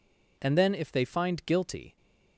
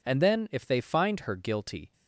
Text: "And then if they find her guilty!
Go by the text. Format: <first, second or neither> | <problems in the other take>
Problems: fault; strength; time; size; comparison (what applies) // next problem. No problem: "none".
second | skips "her"; at 1.4 s